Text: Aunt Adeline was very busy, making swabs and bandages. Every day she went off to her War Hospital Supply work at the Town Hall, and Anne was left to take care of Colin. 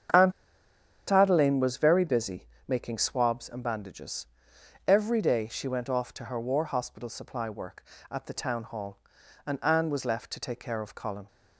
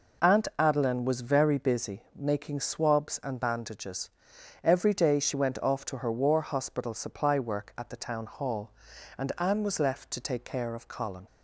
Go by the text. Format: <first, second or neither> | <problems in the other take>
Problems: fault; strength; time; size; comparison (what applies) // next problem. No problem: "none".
second | starts louder than the rest; strong; until 1.9 s; 8 dB // pauses between "Aunt" and "Adeline"; noticeable; at 0.3 s; 0.77 s long